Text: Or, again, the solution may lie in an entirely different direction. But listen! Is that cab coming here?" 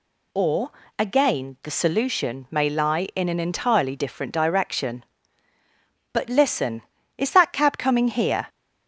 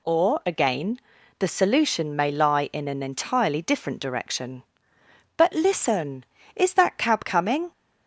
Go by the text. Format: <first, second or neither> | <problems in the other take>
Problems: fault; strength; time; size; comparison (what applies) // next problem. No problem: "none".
first | stops before "here"; at 7.7 s